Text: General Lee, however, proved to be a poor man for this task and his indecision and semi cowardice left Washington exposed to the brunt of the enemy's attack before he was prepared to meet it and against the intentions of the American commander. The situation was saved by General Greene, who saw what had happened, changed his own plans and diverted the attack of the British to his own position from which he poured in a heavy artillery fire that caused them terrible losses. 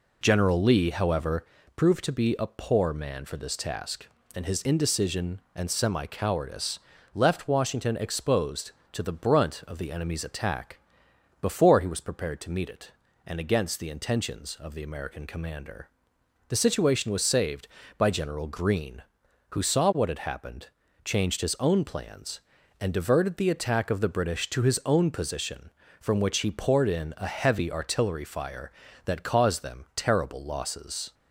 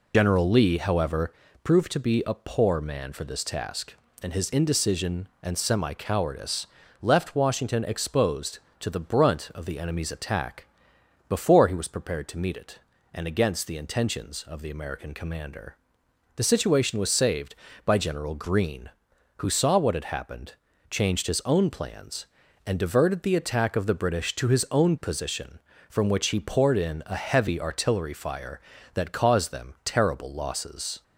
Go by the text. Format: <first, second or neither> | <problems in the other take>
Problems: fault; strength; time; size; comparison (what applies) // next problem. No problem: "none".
first | loses the start of "General"; at 0.1 s; 50 ms // pauses between "cowardice" and "left"; slight; at 6.6 s; 0.36 s long; slight in the first // pauses between "attack" and "before"; noticeable; at 10.6 s; 0.62 s long; noticeable in the first